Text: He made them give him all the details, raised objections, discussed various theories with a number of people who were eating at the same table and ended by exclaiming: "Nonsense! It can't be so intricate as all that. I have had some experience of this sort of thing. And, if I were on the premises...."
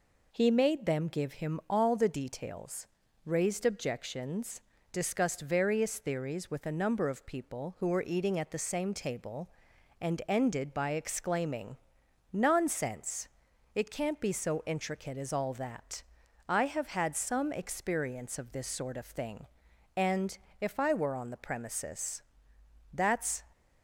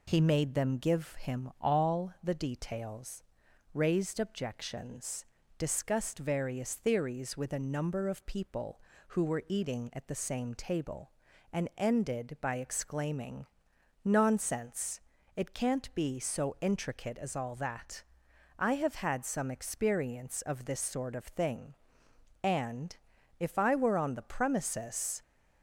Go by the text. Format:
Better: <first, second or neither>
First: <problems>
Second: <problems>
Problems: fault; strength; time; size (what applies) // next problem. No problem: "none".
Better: second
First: goes on to say "That's"; from 22.9 s on; 0.50 s long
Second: none